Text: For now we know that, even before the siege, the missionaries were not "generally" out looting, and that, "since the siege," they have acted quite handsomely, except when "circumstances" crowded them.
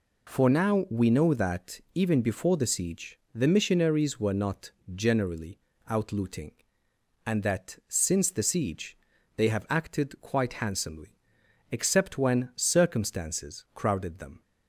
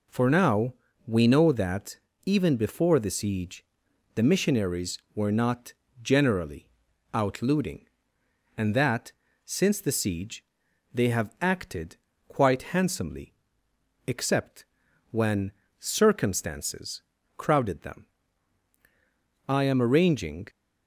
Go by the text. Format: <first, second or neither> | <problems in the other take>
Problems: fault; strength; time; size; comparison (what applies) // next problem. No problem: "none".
first | pauses between "now" and "we"; slight; at 0.7 s; 0.34 s long // pauses between "not" and "generally"; slight; at 5.7 s; 0.28 s long; slight in the first // pauses between "generally" and "out"; noticeable; at 6.6 s; 0.46 s long; slight in the first // pauses between "acted" and "quite"; slight; at 11.9 s; 0.30 s long // pauses between "except" and "when"; noticeable; at 14.6 s; 0.46 s long // pauses between "when" and "circumstances"; slight; at 15.5 s; 0.28 s long // pauses between "circumstances" and "crowded"; slight; at 17.0 s; 0.36 s long // goes on to say "I am arranging"; noticeable; from 19.4 s on; 1.0 s long